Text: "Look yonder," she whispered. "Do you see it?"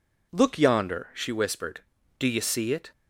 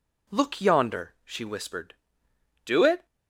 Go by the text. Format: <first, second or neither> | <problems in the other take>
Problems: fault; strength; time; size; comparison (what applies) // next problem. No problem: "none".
first | skips "you see"; at 2.8 s